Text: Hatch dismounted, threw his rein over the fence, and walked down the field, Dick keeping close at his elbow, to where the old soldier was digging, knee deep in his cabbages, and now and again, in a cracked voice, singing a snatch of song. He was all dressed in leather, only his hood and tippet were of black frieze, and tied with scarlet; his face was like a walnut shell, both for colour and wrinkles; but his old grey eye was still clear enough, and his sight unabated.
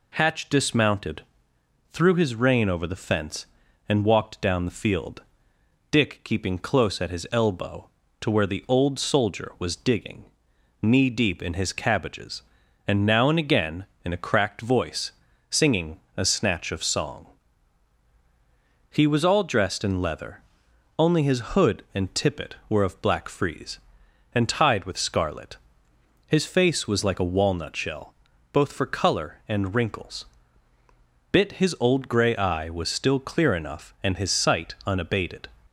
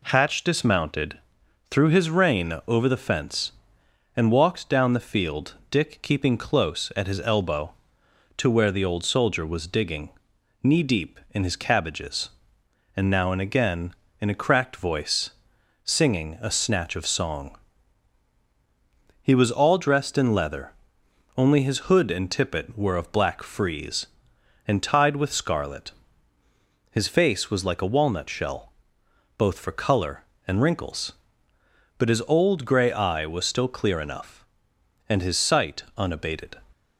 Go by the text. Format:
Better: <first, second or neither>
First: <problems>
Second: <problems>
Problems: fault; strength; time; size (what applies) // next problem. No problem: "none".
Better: second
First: pauses between "singing" and "a"; slight; at 15.9 s; 0.16 s long // says "bit" for "but"; at 31.3 s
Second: none